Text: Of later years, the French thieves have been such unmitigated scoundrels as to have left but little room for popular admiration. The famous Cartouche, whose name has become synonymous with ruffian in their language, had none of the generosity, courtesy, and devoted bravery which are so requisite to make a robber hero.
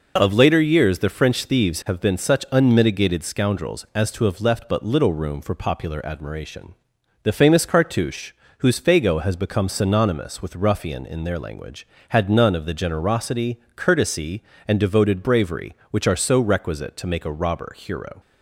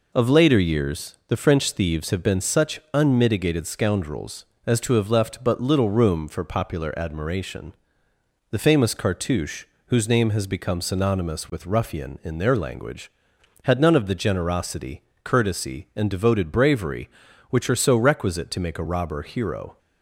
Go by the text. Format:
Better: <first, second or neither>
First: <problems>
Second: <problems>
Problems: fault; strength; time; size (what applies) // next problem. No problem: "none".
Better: second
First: says "fago" for "name"; at 8.8 s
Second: none